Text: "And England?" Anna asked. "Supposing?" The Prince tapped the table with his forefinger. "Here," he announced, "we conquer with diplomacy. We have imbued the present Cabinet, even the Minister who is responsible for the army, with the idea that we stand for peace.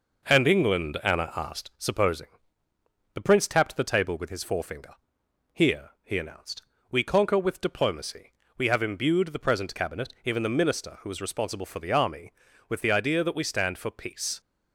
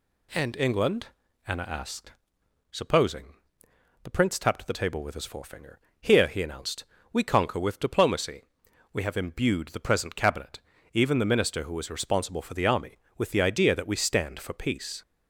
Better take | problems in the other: second | gets quieter; slight; throughout; 2.5 dB

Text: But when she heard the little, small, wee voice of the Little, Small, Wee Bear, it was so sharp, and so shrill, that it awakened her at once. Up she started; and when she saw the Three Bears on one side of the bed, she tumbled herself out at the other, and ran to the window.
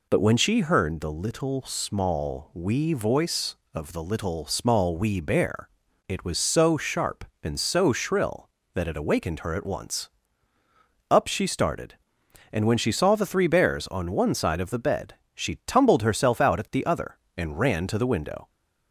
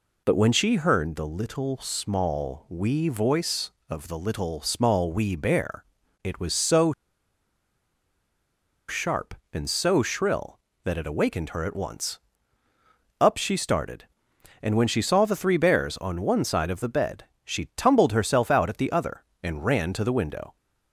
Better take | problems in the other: first | pauses between "so" and "sharp"; strong; at 6.9 s; 1.9 s long

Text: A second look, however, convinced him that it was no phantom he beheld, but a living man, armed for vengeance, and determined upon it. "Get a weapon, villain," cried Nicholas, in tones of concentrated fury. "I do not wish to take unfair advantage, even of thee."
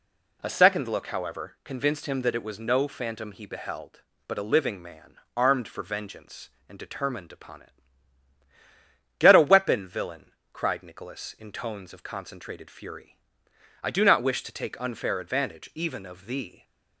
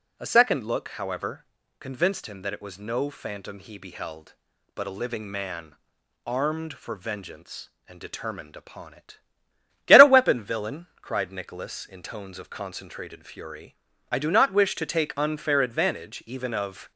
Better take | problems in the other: first | stops before "thee"; at 16.9 s

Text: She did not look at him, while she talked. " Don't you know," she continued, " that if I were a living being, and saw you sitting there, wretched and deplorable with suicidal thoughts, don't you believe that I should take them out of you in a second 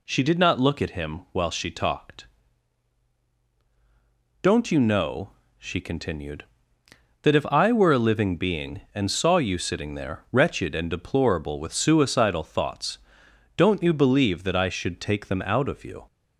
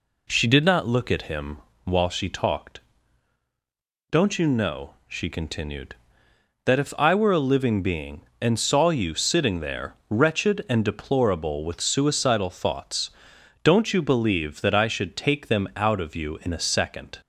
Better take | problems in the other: second | stops before "in a second"; at 16.0 s

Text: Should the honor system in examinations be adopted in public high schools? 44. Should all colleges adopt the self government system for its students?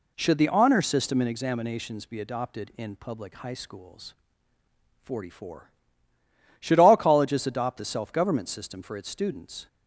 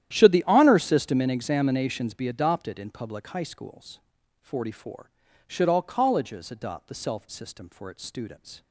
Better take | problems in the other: first | starts louder than the rest; strong; until 1.1 s; 11.5 dB // skips "government"; at 7.2 s

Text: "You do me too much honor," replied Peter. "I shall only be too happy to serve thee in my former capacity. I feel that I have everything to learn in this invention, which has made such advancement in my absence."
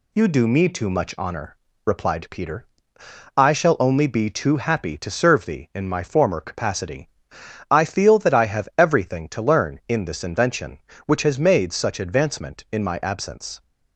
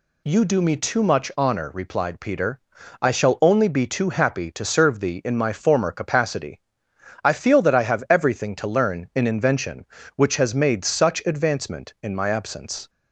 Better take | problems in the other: first | skips "this"; at 9.2 s

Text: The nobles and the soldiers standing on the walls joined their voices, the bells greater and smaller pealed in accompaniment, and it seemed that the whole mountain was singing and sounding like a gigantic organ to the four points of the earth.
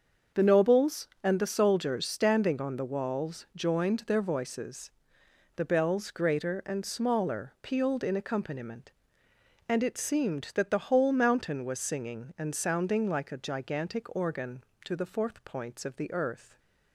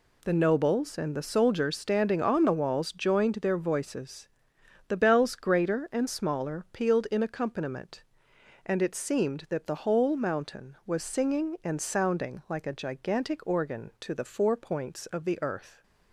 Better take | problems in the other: second | starts louder than the rest; until 1.5 s; 6.5 dB // says "fourth" for "four"; at 15.0 s

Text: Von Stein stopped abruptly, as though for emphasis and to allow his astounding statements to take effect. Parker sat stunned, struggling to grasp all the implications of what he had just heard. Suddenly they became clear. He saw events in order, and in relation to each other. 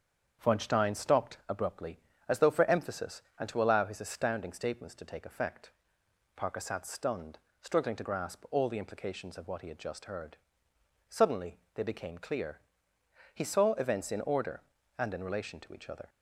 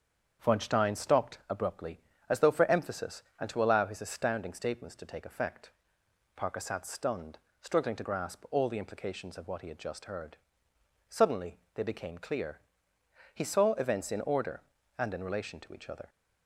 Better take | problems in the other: neither | starts louder than the rest; strong; the same in both // pauses between "Suddenly" and "they"; slight; the same in both

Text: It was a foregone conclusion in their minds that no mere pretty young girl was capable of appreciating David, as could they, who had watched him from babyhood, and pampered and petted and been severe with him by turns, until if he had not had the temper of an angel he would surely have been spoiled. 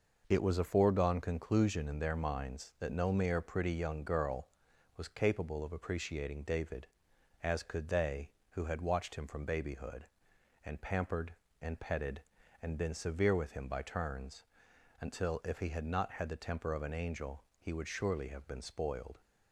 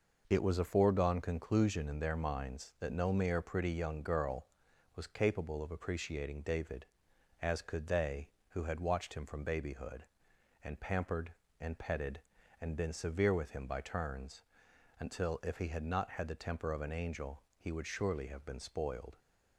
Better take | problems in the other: neither | pauses between "angel" and "he"; slight; the same in both

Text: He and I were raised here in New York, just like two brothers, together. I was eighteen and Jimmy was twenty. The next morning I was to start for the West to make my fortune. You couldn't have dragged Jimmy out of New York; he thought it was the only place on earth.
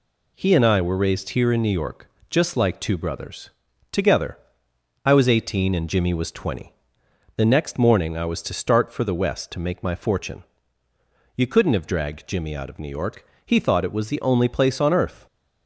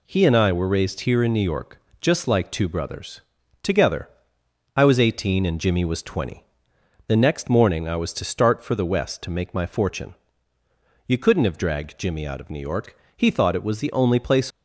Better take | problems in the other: first | stops before "on earth"; at 14.5 s

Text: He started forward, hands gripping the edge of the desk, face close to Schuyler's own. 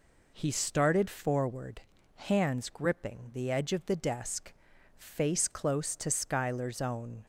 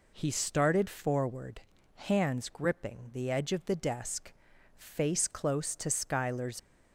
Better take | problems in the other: first | stops before "own"; at 6.5 s

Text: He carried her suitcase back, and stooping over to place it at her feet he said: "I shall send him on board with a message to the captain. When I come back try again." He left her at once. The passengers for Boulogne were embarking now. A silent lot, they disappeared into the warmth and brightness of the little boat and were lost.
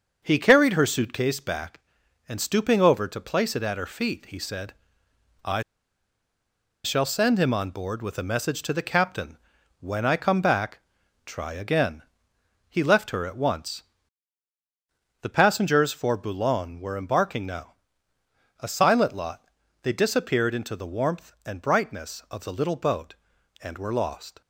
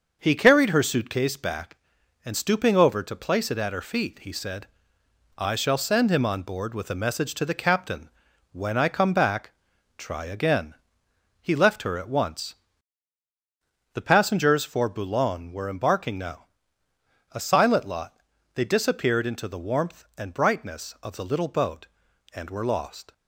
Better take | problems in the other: second | starts louder than the rest; until 1.2 s; 6 dB; also in the second // pauses between "I" and "shall"; at 5.6 s; 1.2 s long // pauses between "back" and "try"; noticeable; at 10.7 s; 0.48 s long; noticeable in the second

